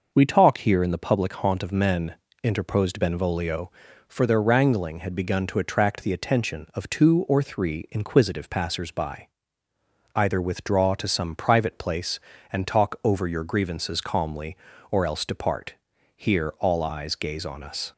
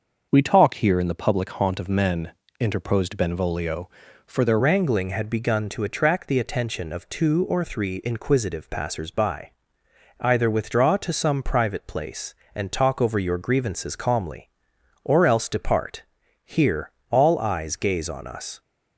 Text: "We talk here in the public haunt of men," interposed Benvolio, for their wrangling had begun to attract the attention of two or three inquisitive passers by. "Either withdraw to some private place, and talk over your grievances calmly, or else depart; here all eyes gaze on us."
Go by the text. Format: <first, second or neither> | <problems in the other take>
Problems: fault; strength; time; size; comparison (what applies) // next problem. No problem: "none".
first | starts louder than the rest; until 1.3 s; 6.5 dB // changes voice at "wrangling"; from 4.5 s on; 14.1 s long // pauses between "here" and "all"; slight; at 16.8 s; 0.22 s long